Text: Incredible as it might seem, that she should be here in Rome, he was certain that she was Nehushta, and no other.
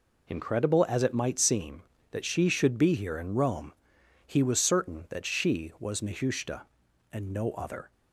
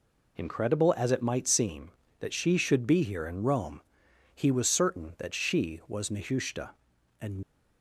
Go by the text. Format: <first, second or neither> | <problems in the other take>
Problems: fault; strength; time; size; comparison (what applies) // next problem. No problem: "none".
first | stops before "no other"; at 7.4 s